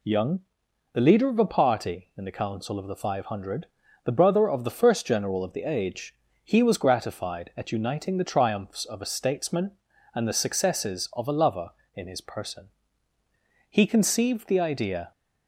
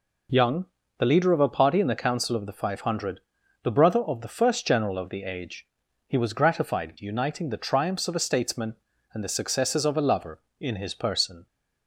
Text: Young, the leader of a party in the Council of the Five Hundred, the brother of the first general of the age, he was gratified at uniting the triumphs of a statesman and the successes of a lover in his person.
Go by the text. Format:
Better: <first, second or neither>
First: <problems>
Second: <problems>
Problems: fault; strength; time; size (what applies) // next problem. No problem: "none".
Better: second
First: goes on to say "He conceived the idea"; from 13.6 s on; 1.4 s long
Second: none